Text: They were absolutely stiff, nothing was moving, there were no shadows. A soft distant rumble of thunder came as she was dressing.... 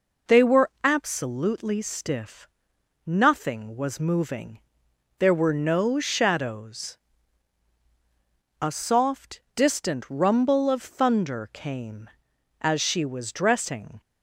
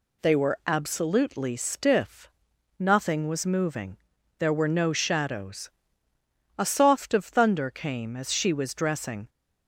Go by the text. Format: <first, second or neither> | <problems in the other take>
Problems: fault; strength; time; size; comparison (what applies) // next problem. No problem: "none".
first | skips "distant rumble"; at 7.1 s